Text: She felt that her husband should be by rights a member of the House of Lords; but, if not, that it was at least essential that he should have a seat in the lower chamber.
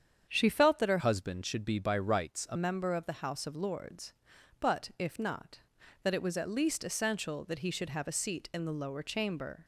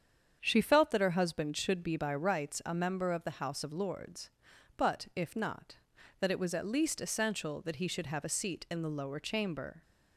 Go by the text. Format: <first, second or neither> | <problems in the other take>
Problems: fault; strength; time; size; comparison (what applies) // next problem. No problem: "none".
second | starts louder than the rest; strong; until 1.3 s; 8 dB; strong in the second // changes voice from "husband" to "a"; from 0.9 to 2.5 s; 1.6 s long